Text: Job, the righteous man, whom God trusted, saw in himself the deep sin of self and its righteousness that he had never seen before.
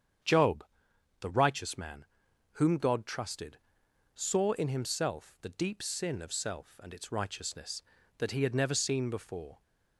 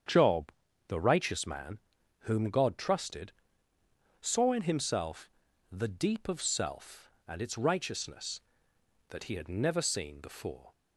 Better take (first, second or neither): first